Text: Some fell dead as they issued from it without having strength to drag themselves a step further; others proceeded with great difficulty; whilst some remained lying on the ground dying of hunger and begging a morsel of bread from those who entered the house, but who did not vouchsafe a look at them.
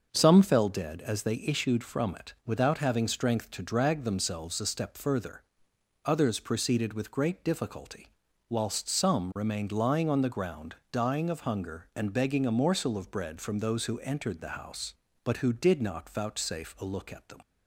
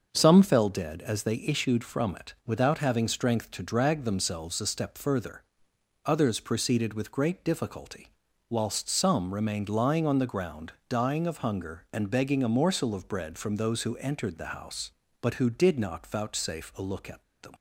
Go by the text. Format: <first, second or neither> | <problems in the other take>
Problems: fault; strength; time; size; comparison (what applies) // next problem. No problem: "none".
first | starts louder than the rest; until 1.1 s; 6 dB; also in the first // pauses between "ground" and "dying"; slight; at 10.7 s; 0.16 s long; slight in the first // pauses between "at" and "them"; slight; at 17.2 s; 0.19 s long